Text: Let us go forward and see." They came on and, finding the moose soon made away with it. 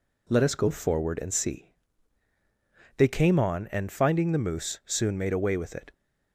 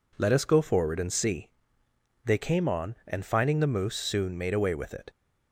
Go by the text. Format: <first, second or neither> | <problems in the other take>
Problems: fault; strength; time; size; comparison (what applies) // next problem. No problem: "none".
neither | none